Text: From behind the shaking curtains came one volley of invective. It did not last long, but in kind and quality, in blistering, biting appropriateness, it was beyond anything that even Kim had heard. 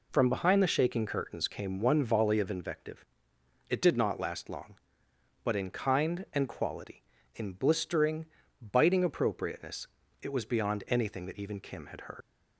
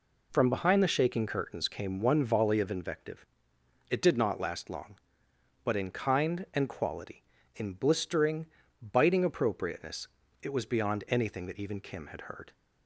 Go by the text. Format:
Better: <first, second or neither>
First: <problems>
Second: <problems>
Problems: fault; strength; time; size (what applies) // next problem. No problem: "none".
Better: second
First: leaves "heard" unfinished; at 12.2 s; 120 ms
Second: none